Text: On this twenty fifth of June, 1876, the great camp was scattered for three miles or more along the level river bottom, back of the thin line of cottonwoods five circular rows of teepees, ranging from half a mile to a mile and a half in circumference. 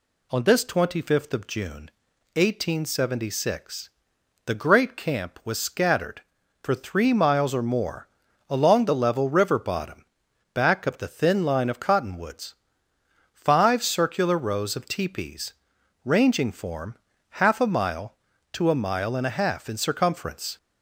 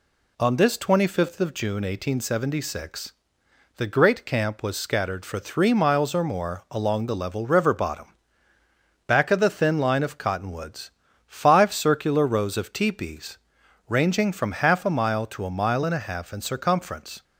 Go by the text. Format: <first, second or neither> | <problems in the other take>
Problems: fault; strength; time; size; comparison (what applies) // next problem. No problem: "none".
second | pauses between "more" and "along"; at 8.0 s; 0.42 s long // pauses between "cottonwoods" and "five"; noticeable; at 12.5 s; 0.78 s long; slight in the second // says "form" for "from"; at 16.4 s